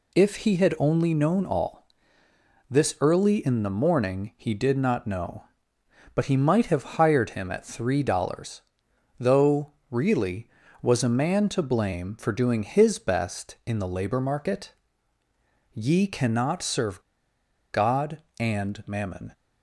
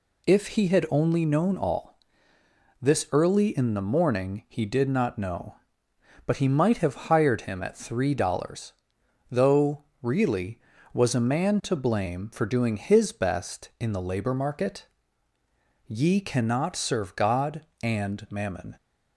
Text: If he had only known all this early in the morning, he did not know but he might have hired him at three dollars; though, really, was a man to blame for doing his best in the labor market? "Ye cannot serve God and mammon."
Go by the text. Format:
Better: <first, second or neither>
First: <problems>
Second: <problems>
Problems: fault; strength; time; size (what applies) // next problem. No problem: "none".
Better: second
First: pauses between "all" and "this"; noticeable; at 1.8 s; 0.84 s long // pauses between "serve" and "God"; noticeable; at 17.0 s; 0.70 s long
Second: pauses between "all" and "this"; noticeable; at 1.9 s; 0.84 s long